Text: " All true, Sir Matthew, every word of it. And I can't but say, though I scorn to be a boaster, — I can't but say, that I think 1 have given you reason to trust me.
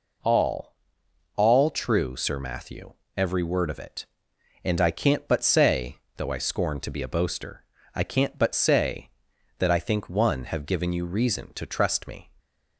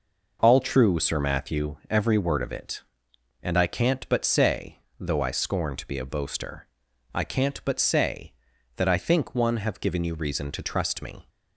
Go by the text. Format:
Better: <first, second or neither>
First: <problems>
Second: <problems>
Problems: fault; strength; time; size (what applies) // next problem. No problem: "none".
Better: second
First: says "All" twice; at 1.3 s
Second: none